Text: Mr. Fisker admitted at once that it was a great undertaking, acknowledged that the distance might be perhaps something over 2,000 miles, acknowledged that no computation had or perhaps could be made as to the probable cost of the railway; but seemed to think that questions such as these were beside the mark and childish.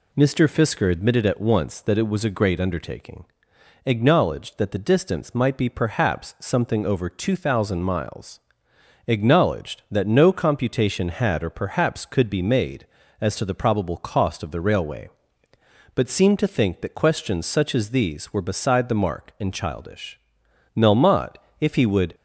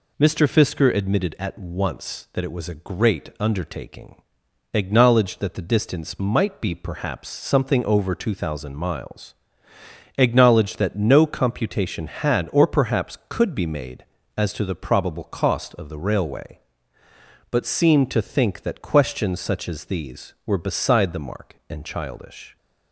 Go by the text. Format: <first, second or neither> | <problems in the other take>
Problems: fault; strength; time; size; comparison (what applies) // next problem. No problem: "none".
second | goes on to say "Melmotte if he would"; from 20.7 s on; 1.4 s long